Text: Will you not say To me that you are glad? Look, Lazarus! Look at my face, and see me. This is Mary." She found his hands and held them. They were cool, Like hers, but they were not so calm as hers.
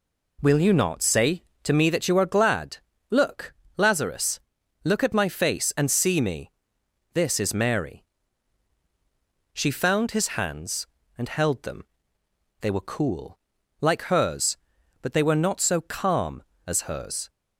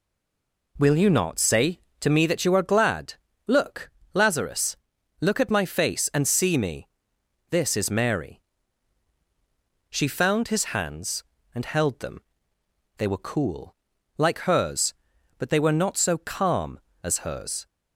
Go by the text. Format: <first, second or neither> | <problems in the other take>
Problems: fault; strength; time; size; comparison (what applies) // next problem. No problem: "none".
first | stays silent before the first word; slight; until 0.7 s; 0.7 s long